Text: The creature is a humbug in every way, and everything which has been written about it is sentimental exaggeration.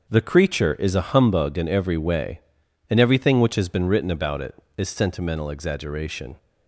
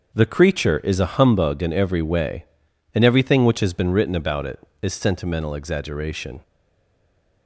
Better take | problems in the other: first | starts louder than the rest; noticeable; until 1.1 s; 6 dB; noticeable in the first // stays silent after the last word; from 6.4 s on; 1.0 s long

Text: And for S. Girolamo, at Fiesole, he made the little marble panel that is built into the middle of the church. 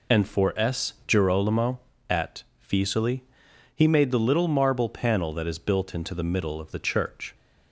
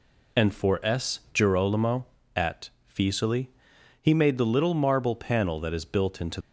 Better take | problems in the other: first | pauses between "at" and "Fiesole"; slight; at 2.6 s; 0.20 s long; slight in the first // stops before "the middle of the church"; at 6.4 s

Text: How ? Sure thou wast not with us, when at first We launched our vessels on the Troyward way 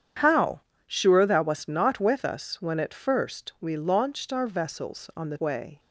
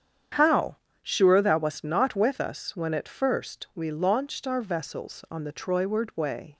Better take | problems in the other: second | starts louder than the rest; strong; until 1.4 s; 8.5 dB; strong in the second // skips "Troyward"; at 5.3 s

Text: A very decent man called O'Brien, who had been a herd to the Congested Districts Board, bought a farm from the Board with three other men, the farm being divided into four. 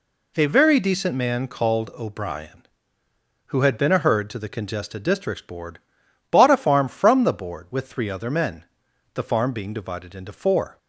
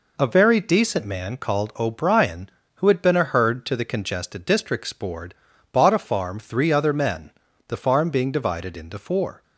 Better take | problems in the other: first | skips "from the Board with"; at 6.3 s

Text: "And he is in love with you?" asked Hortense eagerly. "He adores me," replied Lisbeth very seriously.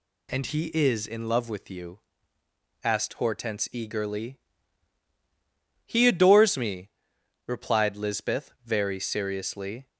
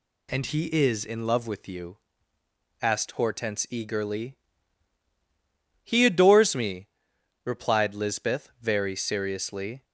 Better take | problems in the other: neither | none

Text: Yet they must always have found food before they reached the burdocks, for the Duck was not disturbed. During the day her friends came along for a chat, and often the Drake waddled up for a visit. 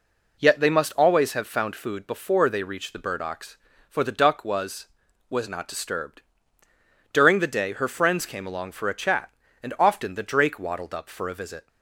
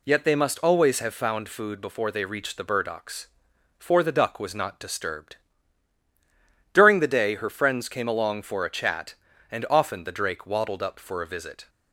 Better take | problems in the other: second | says "was" twice; at 5.2 s

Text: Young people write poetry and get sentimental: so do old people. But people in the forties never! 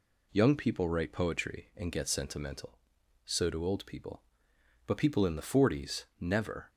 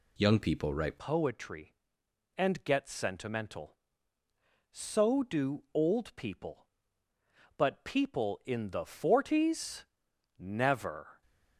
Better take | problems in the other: first | changes voice at "poetry"; from 0.9 s on; 10.3 s long // pauses between "forties" and "never"; noticeable; at 9.8 s; 0.52 s long; slight in the first

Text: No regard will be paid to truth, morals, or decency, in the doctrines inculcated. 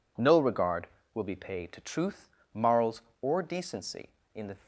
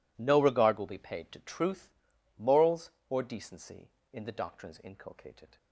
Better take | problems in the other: second | stops before "doctrines inculcated"; at 4.6 s

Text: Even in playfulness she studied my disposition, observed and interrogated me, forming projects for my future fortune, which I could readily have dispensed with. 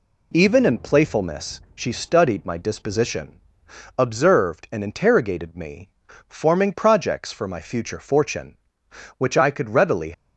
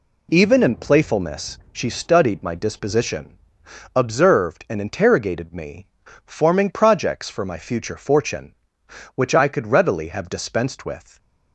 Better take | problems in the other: second | stops before "have dispensed with"; at 10.1 s

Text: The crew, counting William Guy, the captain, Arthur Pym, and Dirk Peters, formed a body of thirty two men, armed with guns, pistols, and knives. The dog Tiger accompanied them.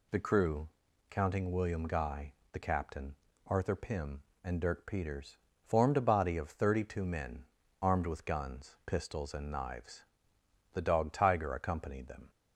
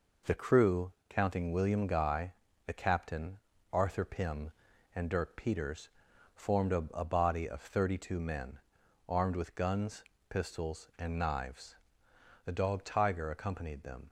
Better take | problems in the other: first | says "a" twice; at 6.9 s

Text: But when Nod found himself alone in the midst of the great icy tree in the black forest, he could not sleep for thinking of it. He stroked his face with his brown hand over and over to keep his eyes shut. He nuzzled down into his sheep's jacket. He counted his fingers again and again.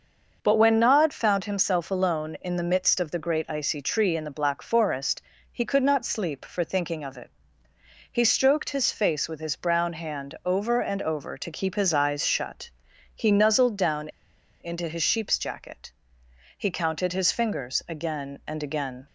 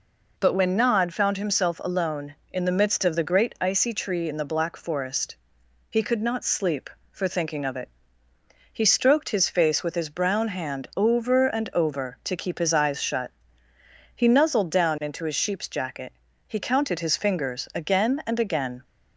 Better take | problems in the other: second | starts louder than the rest; until 1.4 s; 6 dB // pauses between "down" and "into"; noticeable; at 14.0 s; 0.52 s long

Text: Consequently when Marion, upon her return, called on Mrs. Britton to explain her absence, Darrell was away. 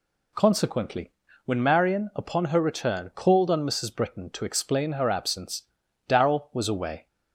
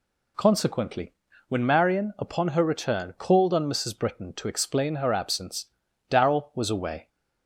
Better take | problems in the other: neither | pauses between "Consequently" and "when"; slight; the same in both

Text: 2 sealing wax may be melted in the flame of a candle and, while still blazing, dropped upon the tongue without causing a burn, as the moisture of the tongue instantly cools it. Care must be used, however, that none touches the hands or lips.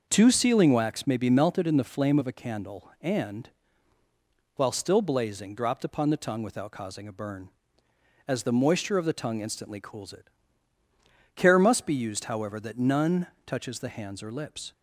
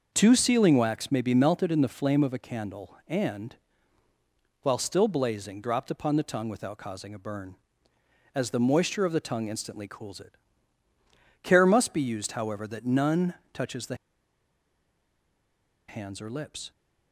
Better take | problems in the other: first | starts louder than the rest; noticeable; until 1.1 s; 6 dB; noticeable in the first // pauses between "none" and "touches"; slight; at 13.3 s; 0.20 s long; slight in the first // pauses between "the" and "hands"; strong; at 13.9 s; 1.9 s long

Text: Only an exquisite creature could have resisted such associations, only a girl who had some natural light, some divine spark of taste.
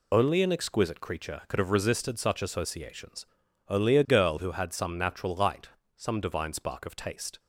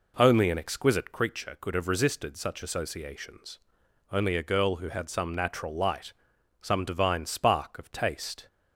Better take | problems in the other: second | loses the start of "Only"; at 0.1 s; 25 ms

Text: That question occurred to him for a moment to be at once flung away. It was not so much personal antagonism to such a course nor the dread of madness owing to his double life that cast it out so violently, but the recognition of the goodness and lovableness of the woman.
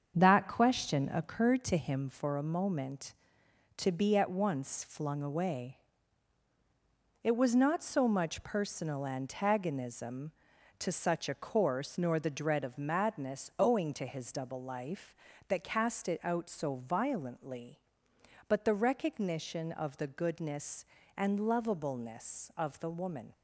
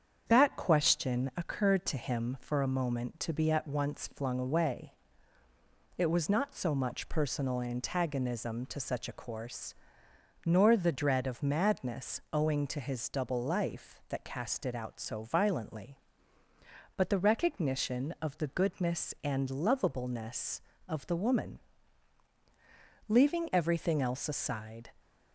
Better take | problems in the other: first | starts louder than the rest; strong; until 1.2 s; 7.5 dB; also in the first // pauses between "course" and "nor"; noticeable; at 9.7 s; 0.72 s long // goes on to say "Leaving everything else aside"; strong; from 23.0 s on; 1.8 s long

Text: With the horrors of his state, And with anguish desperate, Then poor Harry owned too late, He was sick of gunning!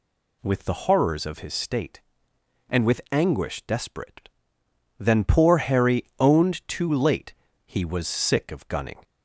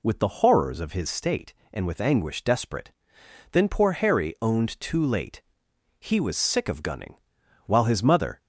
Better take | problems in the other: first | goes on to say "While his mother"; noticeable; from 7.6 s on; 0.74 s long

